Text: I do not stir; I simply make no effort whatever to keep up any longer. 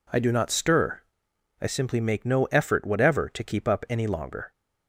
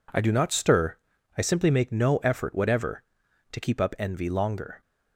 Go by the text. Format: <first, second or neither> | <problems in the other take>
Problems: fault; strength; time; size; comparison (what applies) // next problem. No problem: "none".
first | says "envy" for "any"; at 3.9 s